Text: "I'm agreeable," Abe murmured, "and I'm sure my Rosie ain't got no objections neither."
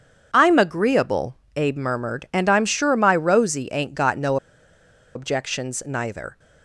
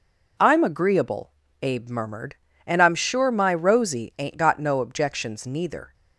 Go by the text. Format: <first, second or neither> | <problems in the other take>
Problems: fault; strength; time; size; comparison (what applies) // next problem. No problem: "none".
second | pauses between "no" and "objections"; noticeable; at 4.3 s; 0.78 s long